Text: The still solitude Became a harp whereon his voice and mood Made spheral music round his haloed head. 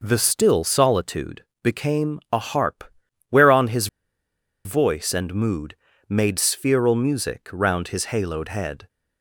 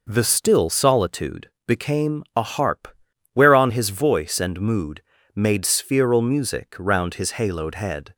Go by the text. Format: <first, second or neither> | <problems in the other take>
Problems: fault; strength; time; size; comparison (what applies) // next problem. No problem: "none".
second | pauses between "solitude" and "Became"; slight; at 1.4 s; 0.18 s long; slight in the second // pauses between "harp" and "whereon"; noticeable; at 2.8 s; 0.48 s long; noticeable in the second // pauses between "his" and "voice"; noticeable; at 3.8 s; 0.78 s long // pauses between "mood" and "Made"; slight; at 5.7 s; 0.34 s long; slight in the second